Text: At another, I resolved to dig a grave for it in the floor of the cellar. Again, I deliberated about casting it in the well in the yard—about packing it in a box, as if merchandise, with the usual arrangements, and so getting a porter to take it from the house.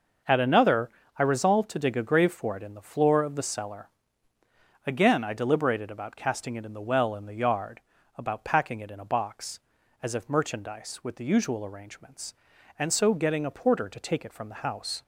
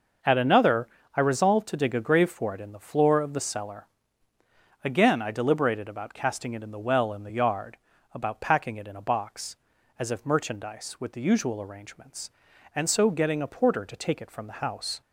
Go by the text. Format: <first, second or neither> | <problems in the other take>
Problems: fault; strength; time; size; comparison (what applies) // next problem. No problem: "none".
neither | starts louder than the rest; the same in both